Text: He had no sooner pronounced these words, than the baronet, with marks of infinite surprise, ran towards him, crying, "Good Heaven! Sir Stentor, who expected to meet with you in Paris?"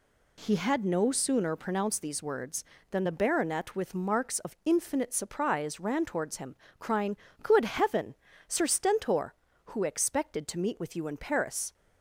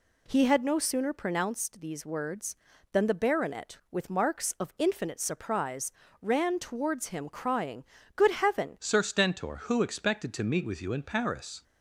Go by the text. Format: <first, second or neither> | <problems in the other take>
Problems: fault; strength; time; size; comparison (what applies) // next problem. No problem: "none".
first | changes voice at "Sir"; from 8.7 s on; 2.9 s long